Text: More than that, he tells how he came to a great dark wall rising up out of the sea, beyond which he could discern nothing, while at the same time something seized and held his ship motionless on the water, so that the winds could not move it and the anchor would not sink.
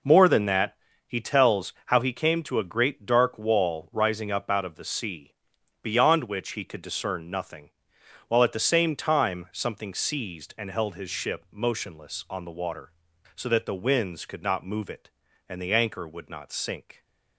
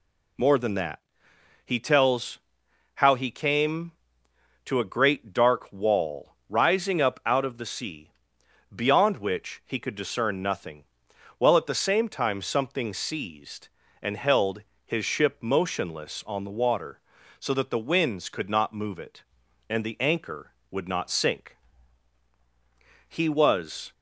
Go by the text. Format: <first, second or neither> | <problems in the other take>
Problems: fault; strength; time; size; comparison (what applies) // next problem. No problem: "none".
first | pauses between "tells" and "how"; noticeable; at 2.3 s; 0.58 s long // pauses between "held" and "his"; slight; at 14.6 s; 0.22 s long // goes on to say "He was"; noticeable; from 23.0 s on; 0.84 s long